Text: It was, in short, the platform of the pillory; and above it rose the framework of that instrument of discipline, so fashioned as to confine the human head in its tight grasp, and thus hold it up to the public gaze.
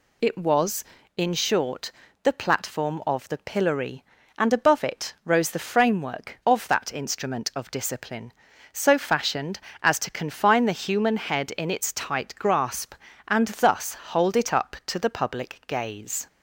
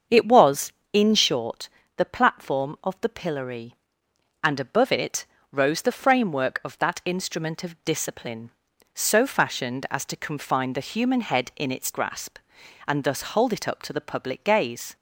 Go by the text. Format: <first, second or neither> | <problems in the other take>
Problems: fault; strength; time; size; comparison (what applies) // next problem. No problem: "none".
first | starts louder than the rest; until 1.3 s; 7 dB // pauses between "it" and "rose"; slight; at 5.2 s; 0.26 s long // skips "tight"; at 11.9 s